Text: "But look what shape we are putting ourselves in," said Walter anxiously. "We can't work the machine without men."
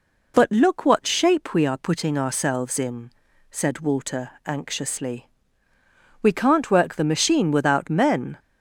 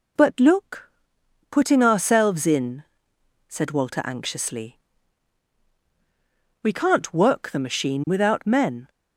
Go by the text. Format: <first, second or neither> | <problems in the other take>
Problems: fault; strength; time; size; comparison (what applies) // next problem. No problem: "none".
first | skips "what shape we are"; at 1.2 s